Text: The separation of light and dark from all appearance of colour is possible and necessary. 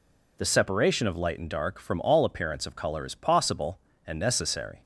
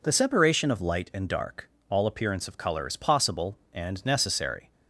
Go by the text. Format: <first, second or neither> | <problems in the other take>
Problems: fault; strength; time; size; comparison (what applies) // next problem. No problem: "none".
first | skips "from"; at 1.7 s